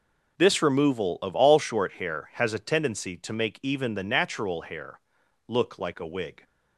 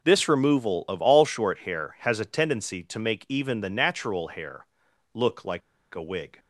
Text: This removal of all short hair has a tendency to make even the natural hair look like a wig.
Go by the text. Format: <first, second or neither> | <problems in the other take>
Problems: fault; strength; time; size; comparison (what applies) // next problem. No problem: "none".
first | pauses between "hair" and "look"; noticeable; at 4.6 s; 0.48 s long; noticeable in the first // pauses between "like" and "a"; slight; at 5.6 s; 0.34 s long